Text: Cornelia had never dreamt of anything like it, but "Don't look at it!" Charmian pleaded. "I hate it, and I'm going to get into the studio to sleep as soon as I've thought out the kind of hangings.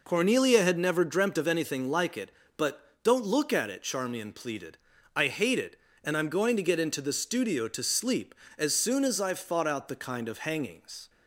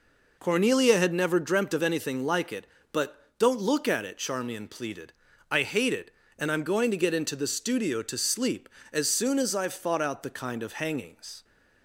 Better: neither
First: none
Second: none

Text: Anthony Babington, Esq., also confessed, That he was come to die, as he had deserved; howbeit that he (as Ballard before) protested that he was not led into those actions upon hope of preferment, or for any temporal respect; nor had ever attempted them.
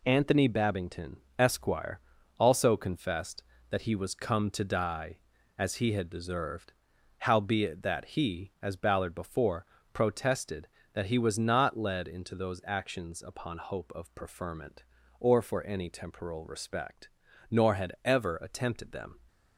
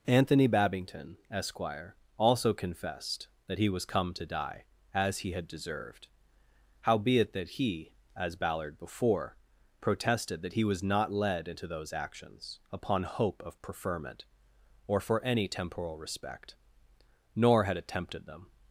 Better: first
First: none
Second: skips "ever"; at 17.7 s

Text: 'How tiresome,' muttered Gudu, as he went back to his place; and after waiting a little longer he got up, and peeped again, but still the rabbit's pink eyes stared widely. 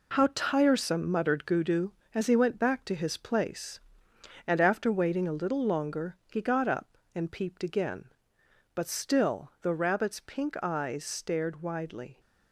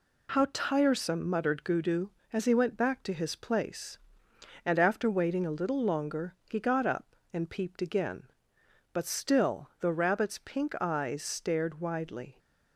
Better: second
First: gets quieter; strong; throughout; 9 dB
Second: none

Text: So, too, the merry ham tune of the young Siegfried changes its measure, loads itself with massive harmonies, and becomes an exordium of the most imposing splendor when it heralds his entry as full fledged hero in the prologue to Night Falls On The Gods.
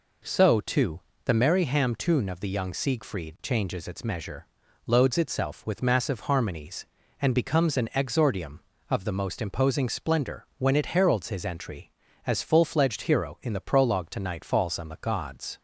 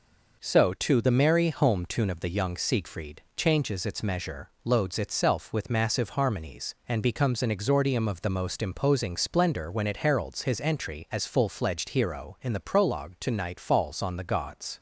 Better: first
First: none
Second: says "home" for "ham"; at 1.4 s

